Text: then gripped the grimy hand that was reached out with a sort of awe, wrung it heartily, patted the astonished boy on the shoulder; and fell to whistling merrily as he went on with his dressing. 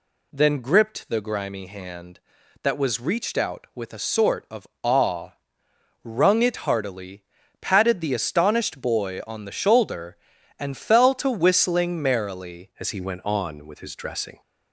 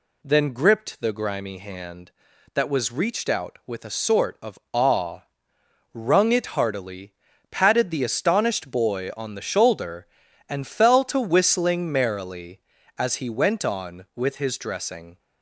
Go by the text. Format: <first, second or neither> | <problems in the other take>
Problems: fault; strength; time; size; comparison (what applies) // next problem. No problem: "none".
second | pauses between "of" and "awe"; slight; at 4.6 s; 0.16 s long // changes voice at "as"; from 12.7 s on; 1.7 s long